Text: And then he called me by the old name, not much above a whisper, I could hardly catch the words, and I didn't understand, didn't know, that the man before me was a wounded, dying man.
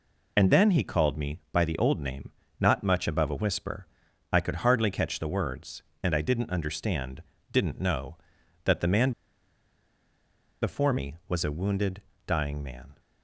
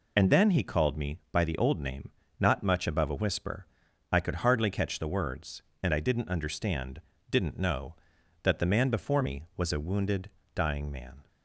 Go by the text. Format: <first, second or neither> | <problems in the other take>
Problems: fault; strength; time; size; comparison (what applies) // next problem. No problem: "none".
second | pauses between "man" and "before"; strong; at 9.1 s; 1.5 s long